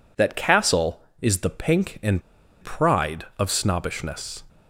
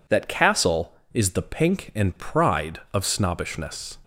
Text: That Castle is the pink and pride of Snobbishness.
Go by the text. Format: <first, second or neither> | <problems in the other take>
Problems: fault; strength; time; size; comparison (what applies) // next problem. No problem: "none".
second | pauses between "and" and "pride"; at 2.2 s; 0.40 s long